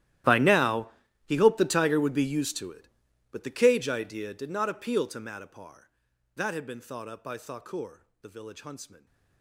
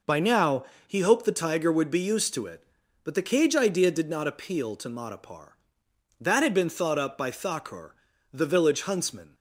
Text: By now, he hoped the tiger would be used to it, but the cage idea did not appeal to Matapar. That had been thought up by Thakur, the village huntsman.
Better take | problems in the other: second | gets quieter; strong; throughout; 22 dB

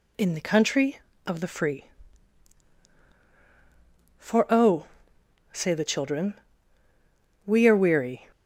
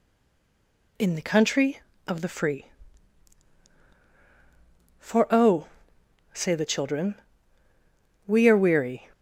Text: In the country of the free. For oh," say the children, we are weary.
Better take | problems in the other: first | stays silent before the first word; until 0.9 s; 0.9 s long

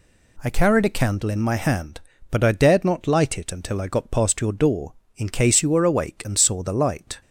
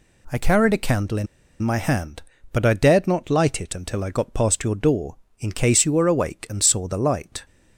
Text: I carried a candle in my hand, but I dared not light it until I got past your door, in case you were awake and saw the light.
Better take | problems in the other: first | pauses between "in" and "my"; slight; at 1.2 s; 0.34 s long

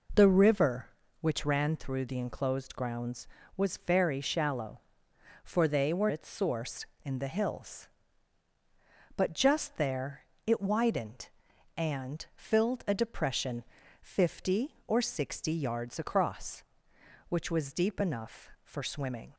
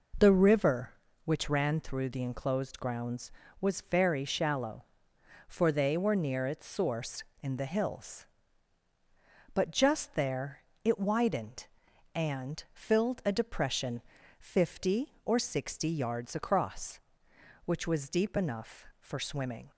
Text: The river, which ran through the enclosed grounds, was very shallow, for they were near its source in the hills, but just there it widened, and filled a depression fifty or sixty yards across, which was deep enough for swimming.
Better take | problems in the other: second | skips "near"; at 6.0 s // pauses between "there" and "it"; slight; at 10.2 s; 0.22 s long; slight in the second // pauses between "depression" and "fifty"; at 13.6 s; 0.38 s long; also in the second

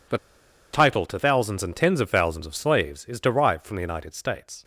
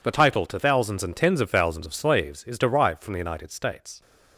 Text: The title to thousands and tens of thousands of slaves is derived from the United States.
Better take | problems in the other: second | pauses between "The" and "title"; noticeable; at 0.1 s; 0.56 s long

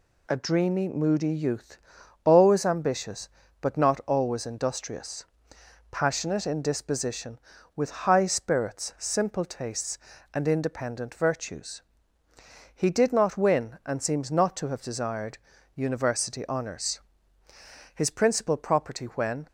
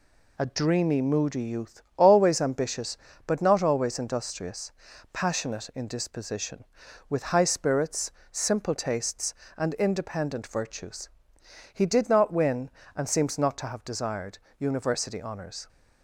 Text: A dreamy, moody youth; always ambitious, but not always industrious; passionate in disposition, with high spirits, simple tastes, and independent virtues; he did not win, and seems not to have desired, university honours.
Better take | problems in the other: second | goes on to say "His principal property when"; from 17.9 s on; 1.5 s long

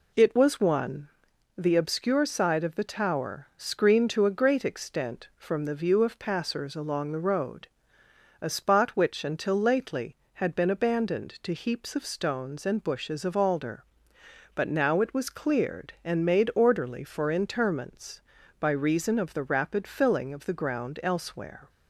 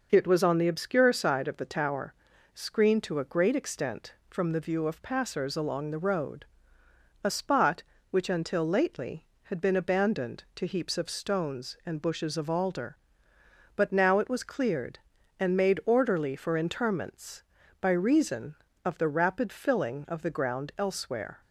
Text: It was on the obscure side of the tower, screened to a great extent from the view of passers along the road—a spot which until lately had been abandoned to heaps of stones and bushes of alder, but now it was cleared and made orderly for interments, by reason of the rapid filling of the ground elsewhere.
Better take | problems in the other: second | says "one" for "on"; at 0.6 s

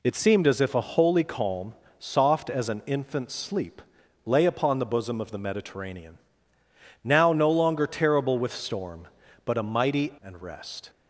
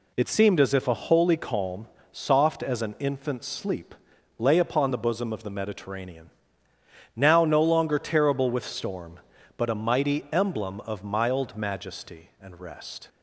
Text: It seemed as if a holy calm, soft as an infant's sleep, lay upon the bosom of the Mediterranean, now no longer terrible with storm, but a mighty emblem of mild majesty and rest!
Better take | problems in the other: second | skips "emblem of mild majesty"; at 10.1 s

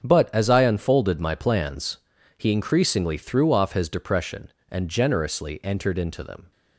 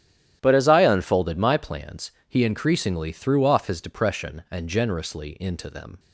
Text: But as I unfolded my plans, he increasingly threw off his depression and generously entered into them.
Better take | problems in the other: first | starts louder than the rest; strong; until 1.4 s; 11.5 dB; strong in the first // skips "entered"; at 5.3 s

